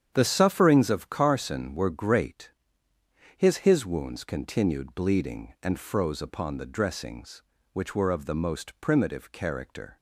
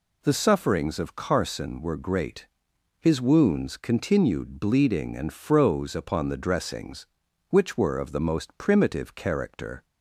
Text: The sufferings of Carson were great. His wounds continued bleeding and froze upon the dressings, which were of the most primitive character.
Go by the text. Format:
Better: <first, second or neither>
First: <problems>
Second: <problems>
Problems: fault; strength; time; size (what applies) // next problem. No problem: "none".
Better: second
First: starts louder than the rest; strong; until 1.1 s; 9 dB // says "His" twice; at 3.6 s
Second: none